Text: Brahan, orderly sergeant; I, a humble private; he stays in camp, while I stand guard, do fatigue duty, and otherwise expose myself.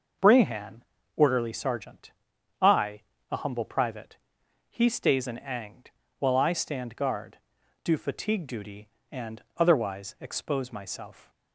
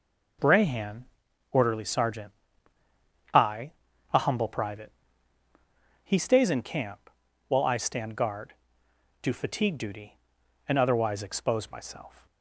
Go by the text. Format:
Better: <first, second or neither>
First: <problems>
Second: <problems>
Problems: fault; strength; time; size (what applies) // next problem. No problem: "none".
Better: second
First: says "angd" for "camp"; at 5.3 s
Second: none